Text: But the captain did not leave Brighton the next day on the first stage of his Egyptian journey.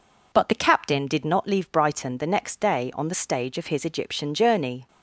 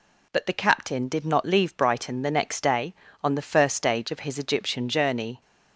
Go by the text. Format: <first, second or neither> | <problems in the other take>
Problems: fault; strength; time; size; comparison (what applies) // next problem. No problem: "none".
second | skips "first"; at 3.1 s